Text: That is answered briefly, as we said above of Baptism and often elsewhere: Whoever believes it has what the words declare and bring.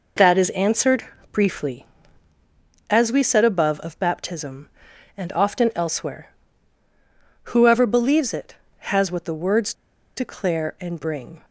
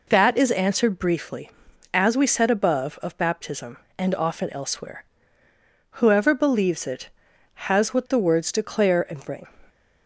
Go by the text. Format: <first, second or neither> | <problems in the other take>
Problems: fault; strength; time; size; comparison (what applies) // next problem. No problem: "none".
second | pauses between "answered" and "briefly"; slight; at 1.0 s; 0.28 s long // pauses between "words" and "declare"; at 9.7 s; 0.42 s long